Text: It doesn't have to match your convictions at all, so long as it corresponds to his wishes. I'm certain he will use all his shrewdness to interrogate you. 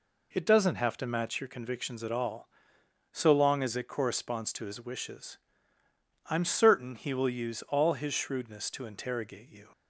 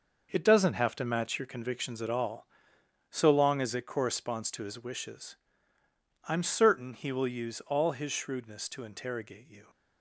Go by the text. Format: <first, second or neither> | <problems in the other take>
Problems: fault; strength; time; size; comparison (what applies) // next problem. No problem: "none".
first | gets quieter; strong; throughout; 8.5 dB